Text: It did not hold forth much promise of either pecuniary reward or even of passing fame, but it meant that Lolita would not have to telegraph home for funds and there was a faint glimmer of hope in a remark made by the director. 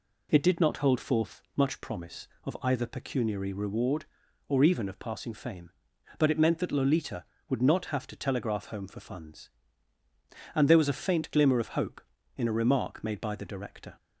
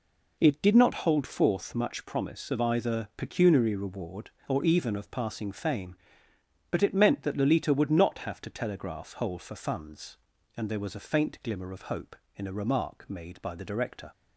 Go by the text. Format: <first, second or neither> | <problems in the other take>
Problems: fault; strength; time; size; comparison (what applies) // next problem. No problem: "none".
first | says "hole" for "home"; at 9.1 s